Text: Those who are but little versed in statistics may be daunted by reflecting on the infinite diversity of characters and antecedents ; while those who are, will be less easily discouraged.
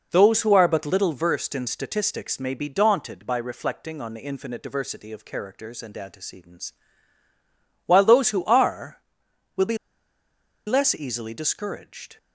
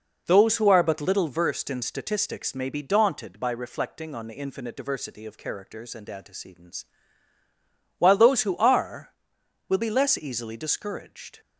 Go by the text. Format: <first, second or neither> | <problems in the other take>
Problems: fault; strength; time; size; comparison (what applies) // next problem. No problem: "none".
second | pauses between "be" and "less"; noticeable; at 9.7 s; 0.89 s long